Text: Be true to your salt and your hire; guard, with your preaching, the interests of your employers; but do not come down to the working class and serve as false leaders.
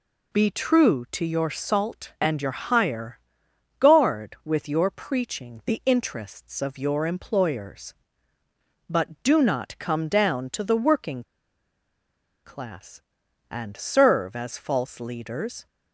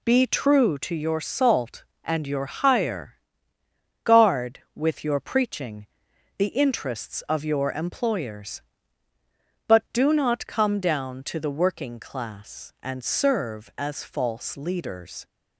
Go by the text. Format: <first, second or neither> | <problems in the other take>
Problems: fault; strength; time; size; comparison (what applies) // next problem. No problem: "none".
second | pauses between "working" and "class"; at 11.2 s; 1.2 s long